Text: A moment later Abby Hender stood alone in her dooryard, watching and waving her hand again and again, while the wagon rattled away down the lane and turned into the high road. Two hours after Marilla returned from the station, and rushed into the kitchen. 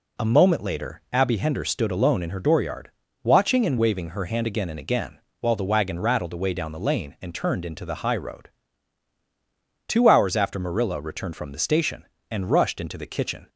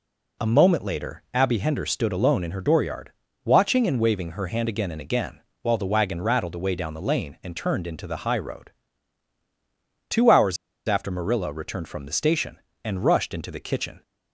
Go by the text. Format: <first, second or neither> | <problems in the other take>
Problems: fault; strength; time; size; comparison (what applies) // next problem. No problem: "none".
first | pauses between "hours" and "after"; slight; at 10.5 s; 0.30 s long